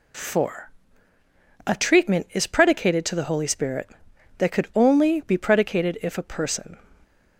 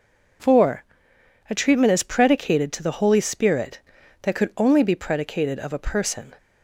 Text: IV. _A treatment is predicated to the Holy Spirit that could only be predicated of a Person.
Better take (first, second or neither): second